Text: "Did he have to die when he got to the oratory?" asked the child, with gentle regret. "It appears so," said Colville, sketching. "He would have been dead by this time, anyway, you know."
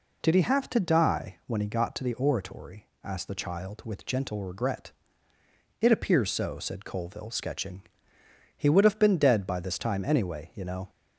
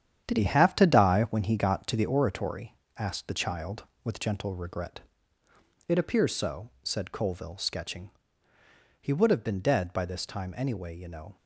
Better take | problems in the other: first | gets quieter; strong; throughout; 8.5 dB

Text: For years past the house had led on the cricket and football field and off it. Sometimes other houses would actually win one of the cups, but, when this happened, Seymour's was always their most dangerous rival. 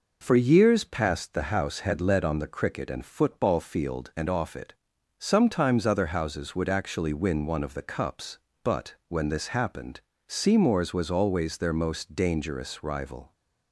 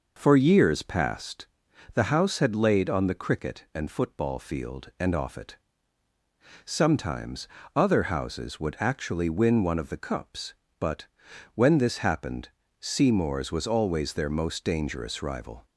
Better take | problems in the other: first | pauses between "past" and "the"; noticeable; at 1.4 s; 0.48 s long // says "laid" for "led"; at 2.5 s // pauses between "Sometimes" and "other"; slight; at 7.4 s; 0.28 s long

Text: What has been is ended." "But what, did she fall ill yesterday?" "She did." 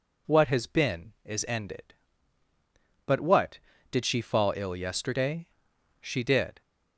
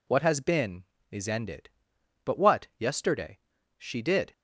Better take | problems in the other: first | skips "did she fall ill"; at 2.7 s

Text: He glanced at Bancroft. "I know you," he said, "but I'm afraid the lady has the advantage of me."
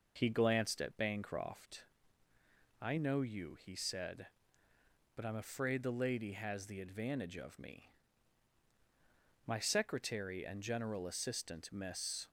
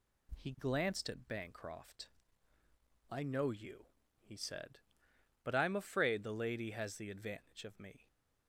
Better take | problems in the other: second | goes on to say "My secretary and general assistant Miss"; strong; from 9.4 s on; 2.8 s long

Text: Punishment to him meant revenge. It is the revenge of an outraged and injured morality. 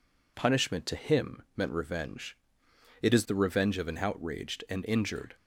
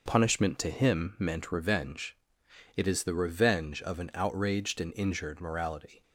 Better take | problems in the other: second | stops before "morality"; at 5.3 s

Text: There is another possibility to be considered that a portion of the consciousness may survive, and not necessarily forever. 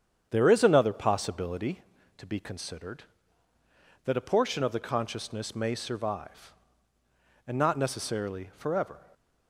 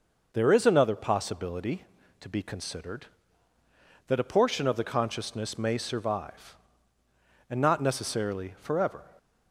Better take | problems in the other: second | starts louder than the rest; strong; until 1.8 s; 8.5 dB

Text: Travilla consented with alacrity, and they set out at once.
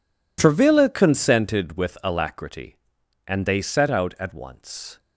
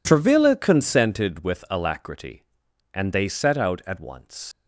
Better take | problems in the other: first | leaves "once" unfinished; at 4.5 s; 155 ms

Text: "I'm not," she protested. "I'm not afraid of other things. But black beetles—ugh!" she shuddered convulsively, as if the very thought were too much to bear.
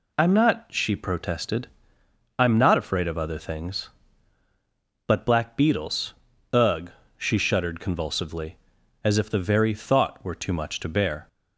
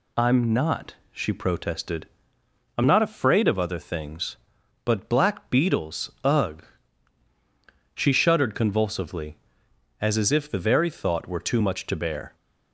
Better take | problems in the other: first | says "as" twice; at 10.1 s

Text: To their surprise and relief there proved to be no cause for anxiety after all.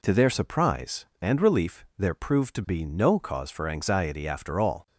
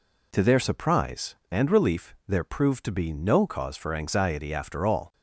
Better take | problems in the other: neither | none

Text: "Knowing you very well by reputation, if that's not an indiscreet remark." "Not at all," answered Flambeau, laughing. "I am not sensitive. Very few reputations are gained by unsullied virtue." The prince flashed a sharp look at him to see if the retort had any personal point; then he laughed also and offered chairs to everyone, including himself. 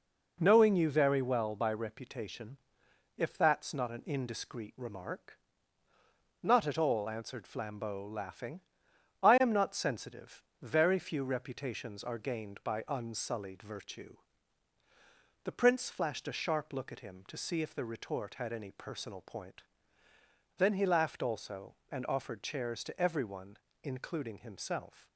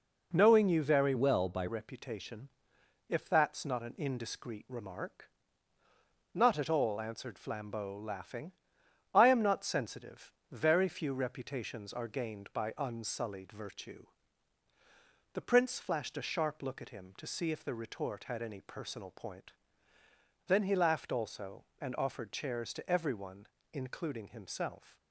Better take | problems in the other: first | changes voice from "well" to "by"; from 1.1 to 1.6 s; 0.5 s long

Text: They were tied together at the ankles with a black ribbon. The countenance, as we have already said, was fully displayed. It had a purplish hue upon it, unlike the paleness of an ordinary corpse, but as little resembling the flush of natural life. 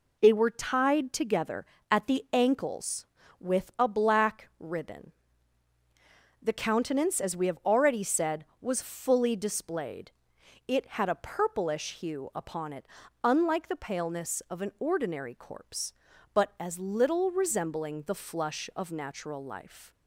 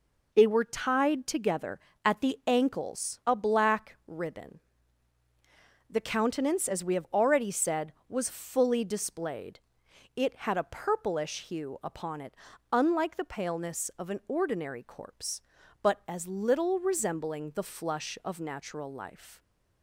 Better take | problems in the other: first | skips "with"; at 3.2 s

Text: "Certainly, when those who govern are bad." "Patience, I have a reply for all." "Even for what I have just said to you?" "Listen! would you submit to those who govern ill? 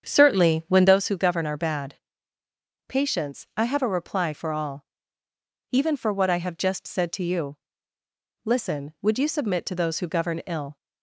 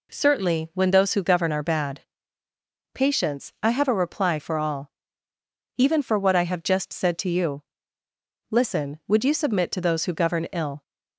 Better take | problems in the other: second | starts louder than the rest; strong; until 1.0 s; 8 dB

